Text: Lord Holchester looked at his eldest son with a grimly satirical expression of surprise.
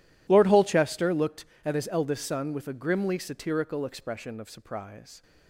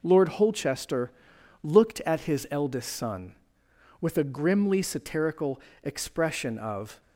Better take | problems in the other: first | pauses between "Holchester" and "looked"; noticeable; at 1.1 s; 0.52 s long // pauses between "satirical" and "expression"; slight; at 5.6 s; 0.22 s long // stops before "surprise"; at 7.0 s

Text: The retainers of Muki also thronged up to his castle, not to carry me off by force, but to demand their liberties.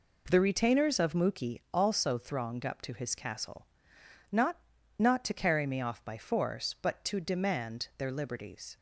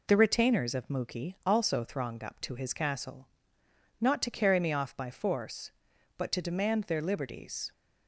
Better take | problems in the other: second | says "not" twice; at 4.9 s

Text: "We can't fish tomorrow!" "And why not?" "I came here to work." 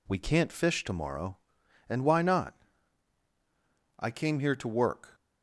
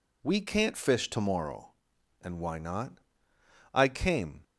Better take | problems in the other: first | stops before "here to work"; at 4.4 s

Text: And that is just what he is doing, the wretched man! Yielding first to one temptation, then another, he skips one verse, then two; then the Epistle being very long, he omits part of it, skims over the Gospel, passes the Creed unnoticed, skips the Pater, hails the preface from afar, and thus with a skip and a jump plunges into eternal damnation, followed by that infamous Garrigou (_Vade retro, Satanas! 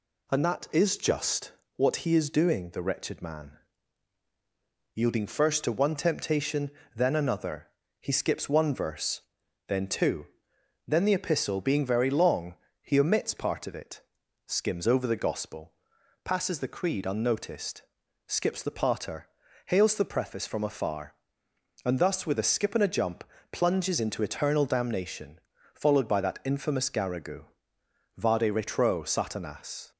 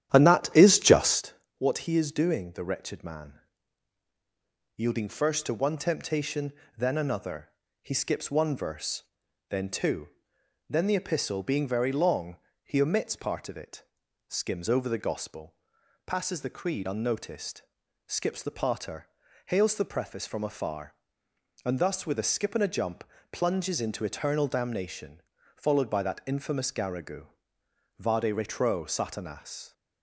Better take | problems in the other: first | starts louder than the rest; strong; until 1.2 s; 11 dB // pauses between "just" and "what"; slight; at 1.3 s; 0.24 s long; slight in the first // pauses between "jump" and "plunges"; slight; at 23.0 s; 0.28 s long; slight in the first

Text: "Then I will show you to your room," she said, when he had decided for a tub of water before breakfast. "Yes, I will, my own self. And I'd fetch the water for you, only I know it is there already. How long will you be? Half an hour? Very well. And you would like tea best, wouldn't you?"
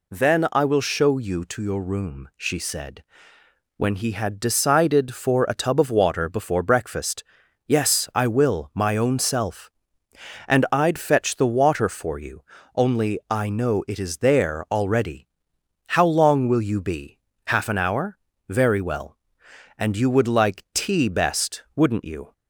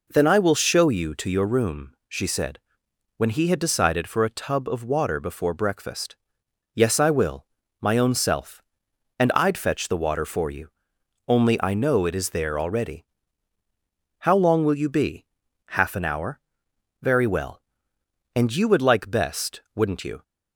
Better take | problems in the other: first | skips "tea"; at 19.1 s

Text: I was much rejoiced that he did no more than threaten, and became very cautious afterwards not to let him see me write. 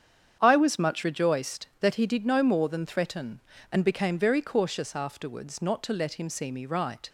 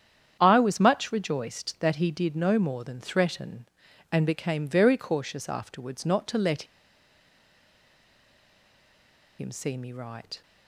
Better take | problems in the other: first | starts louder than the rest; strong; until 1.4 s; 8.5 dB; strong in the first // pauses between "let" and "him"; strong; at 6.6 s; 2.7 s long

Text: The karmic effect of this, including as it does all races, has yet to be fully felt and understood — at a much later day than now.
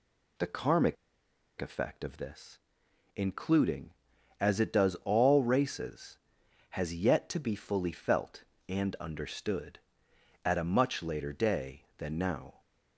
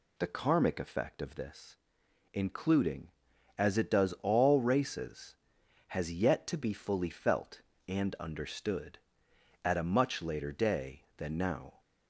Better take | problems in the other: second | pauses between "karmic" and "effect"; noticeable; at 0.9 s; 0.65 s long

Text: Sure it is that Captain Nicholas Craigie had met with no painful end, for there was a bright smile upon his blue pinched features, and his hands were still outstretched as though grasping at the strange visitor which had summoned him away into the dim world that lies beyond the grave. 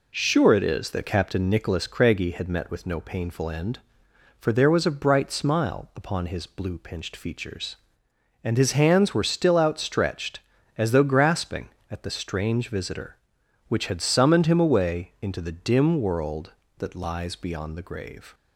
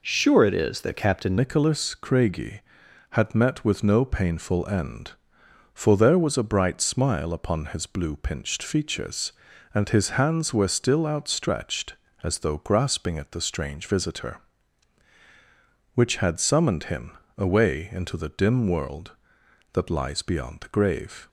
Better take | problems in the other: first | changes voice at "Nicholas"; from 1.3 s on; 19.9 s long // pauses between "him" and "away"; slight; at 17.1 s; 0.22 s long

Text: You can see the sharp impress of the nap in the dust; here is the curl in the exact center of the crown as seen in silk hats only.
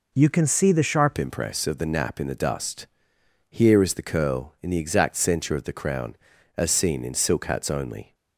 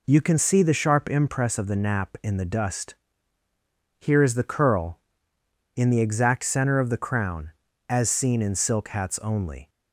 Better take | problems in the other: second | changes voice at "impress"; from 1.1 s on; 7.0 s long

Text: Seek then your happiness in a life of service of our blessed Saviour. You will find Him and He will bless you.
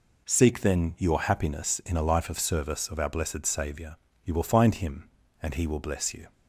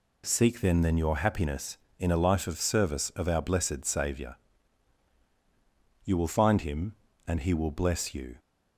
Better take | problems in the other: first | says "then" twice; at 0.8 s

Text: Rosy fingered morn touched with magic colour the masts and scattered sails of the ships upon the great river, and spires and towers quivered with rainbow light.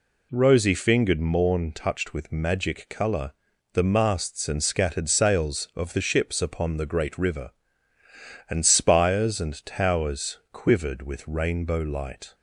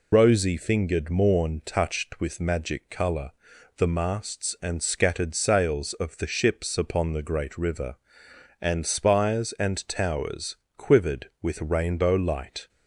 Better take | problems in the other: first | loses the start of "Rosy"; at 0.1 s; 90 ms // pauses between "colour" and "the"; noticeable; at 3.3 s; 0.48 s long; also in the first // pauses between "towers" and "quivered"; slight; at 10.5 s; 0.22 s long

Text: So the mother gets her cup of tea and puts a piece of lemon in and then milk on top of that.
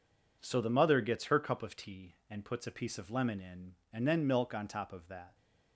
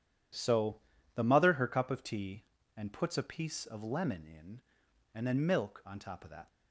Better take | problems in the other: first | pauses between "So" and "the"; slight; at 0.7 s; 0.36 s long // skips "gets"; at 1.5 s

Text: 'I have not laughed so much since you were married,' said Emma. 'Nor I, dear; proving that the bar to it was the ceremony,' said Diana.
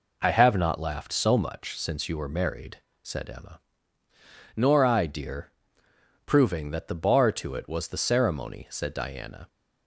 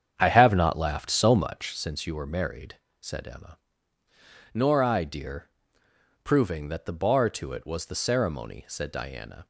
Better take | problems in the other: first | starts louder than the rest; strong; until 1.8 s; 8 dB

